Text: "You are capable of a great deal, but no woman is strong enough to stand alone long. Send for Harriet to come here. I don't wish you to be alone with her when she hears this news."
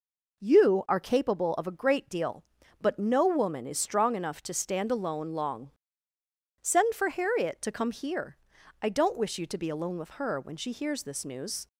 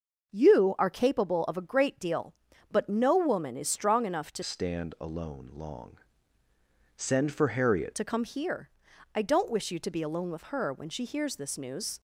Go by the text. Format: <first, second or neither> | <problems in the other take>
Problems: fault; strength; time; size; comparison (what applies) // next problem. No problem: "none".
first | starts louder than the rest; noticeable; until 1.3 s; 6 dB // changes voice from "stand" to "Harriet"; from 4.4 to 7.9 s; 3.5 s long